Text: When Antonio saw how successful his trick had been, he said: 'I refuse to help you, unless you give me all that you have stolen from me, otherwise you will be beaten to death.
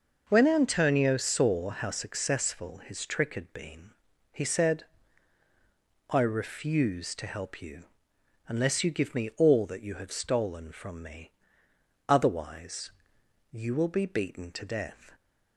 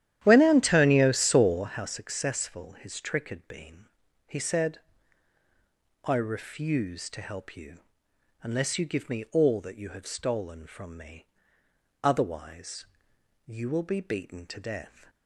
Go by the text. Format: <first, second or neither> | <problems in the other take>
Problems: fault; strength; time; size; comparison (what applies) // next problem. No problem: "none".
first | starts louder than the rest; strong; until 1.7 s; 11.5 dB // pauses between "otherwise" and "you"; noticeable; at 12.8 s; 0.60 s long; noticeable in the first